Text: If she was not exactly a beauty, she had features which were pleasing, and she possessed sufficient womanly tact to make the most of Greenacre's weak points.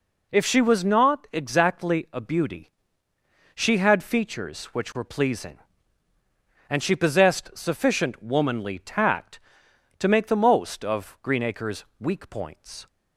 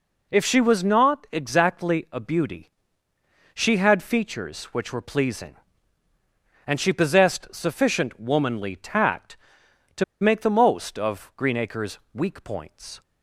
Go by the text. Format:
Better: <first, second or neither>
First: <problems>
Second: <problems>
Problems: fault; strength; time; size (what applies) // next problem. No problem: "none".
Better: first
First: pauses between "Greenacre's" and "weak"; slight; at 11.8 s; 0.16 s long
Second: pauses between "to" and "make"; slight; at 10.0 s; 0.17 s long // pauses between "Greenacre's" and "weak"; slight; at 11.9 s; 0.16 s long